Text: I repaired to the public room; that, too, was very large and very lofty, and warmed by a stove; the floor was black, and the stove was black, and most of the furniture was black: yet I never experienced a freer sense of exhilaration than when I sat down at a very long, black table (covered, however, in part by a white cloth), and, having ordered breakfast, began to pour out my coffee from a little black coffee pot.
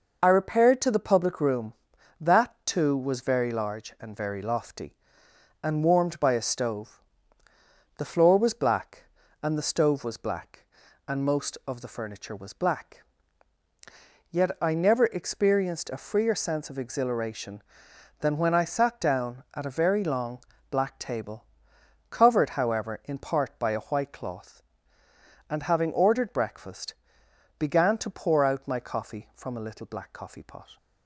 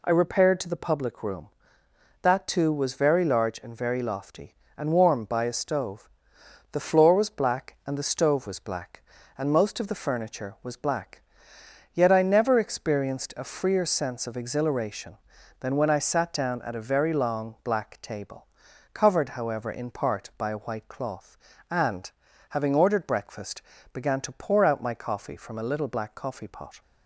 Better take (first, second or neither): neither